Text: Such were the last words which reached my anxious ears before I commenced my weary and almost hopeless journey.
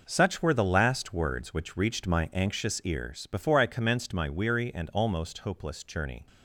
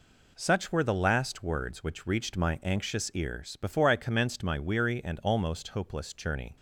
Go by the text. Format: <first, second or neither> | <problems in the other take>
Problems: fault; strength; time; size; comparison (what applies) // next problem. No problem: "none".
second | gets quieter; strong; throughout; 10 dB